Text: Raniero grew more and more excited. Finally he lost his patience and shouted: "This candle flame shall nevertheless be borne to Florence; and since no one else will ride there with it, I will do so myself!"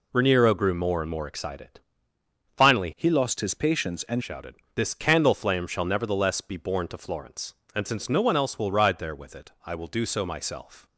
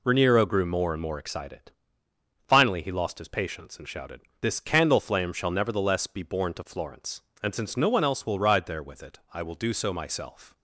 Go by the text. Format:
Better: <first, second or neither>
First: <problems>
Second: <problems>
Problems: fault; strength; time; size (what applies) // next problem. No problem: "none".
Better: second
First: changes voice from "he" to "and"; from 2.9 to 4.2 s; 1.3 s long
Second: none